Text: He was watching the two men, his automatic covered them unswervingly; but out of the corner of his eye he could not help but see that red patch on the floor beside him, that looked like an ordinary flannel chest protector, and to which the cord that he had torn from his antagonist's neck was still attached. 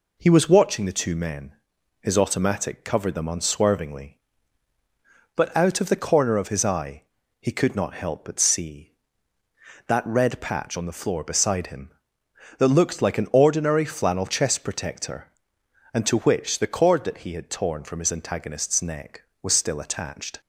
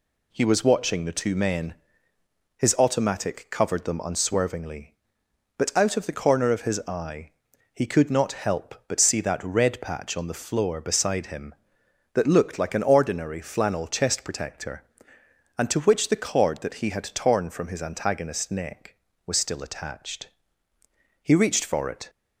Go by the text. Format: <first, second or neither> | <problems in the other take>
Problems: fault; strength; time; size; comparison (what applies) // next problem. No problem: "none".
first | pauses between "eye" and "he"; at 7.3 s; 0.42 s long; slight in the first // goes on to say "He reached for it"; noticeable; from 21.2 s on; 0.86 s long